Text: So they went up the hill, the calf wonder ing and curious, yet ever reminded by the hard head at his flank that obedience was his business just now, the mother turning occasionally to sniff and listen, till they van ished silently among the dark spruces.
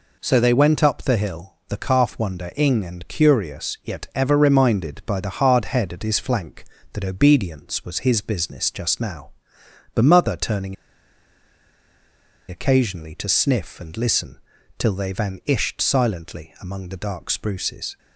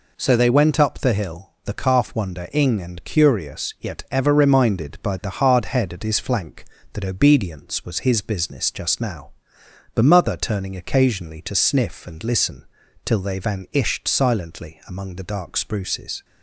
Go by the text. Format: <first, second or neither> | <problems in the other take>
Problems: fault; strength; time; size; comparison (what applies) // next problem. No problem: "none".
second | pauses between "turning" and "occasionally"; strong; at 10.7 s; 1.7 s long